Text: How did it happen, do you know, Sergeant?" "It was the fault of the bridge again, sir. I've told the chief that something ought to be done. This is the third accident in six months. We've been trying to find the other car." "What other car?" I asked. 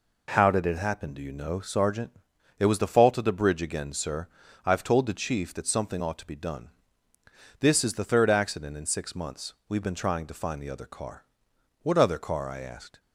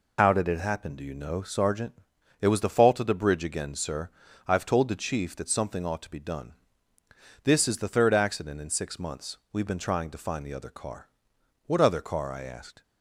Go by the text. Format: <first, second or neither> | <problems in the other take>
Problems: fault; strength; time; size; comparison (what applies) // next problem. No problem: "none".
first | loses the start of "How"; at 0.1 s; 80 ms